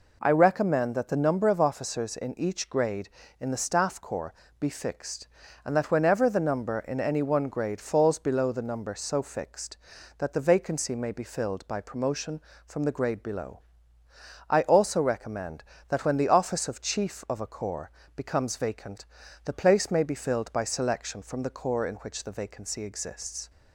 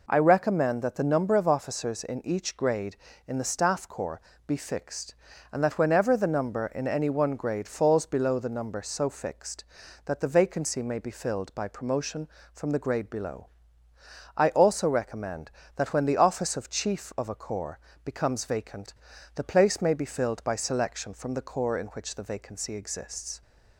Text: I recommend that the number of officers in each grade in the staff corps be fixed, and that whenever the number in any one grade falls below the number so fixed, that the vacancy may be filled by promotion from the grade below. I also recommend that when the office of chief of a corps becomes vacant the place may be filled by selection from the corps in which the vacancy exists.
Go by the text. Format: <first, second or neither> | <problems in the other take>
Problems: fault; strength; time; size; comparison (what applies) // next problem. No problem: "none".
neither | pauses between "corps" and "be"; slight; the same in both // pauses between "corps" and "becomes"; slight; the same in both // pauses between "vacant" and "the"; the same in both